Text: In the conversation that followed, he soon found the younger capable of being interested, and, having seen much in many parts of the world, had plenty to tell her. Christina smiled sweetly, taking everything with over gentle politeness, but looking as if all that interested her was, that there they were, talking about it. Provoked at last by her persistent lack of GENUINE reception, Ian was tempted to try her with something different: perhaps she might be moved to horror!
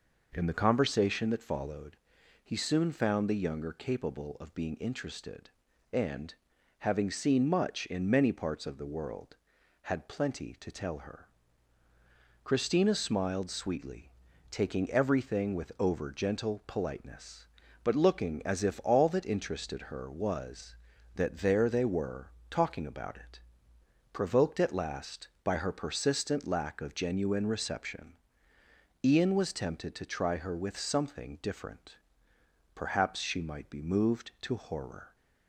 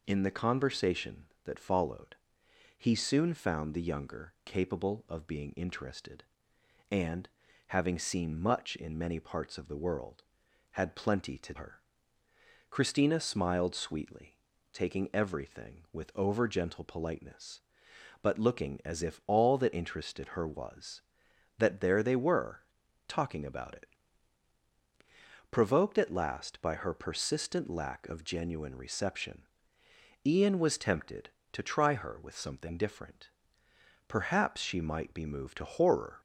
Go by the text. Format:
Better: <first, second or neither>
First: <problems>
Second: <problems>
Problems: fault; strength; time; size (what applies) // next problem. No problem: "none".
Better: first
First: none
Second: skips "tell"; at 11.5 s